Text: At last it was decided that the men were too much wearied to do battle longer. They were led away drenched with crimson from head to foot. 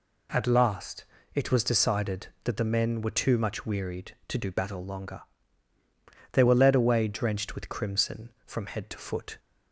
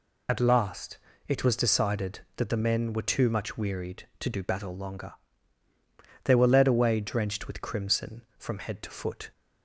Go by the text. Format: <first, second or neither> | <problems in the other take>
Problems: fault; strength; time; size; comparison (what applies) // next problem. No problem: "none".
first | loses the start of "At"; at 0.2 s; 65 ms // pauses between "last" and "it"; slight; at 0.9 s; 0.32 s long; slight in the first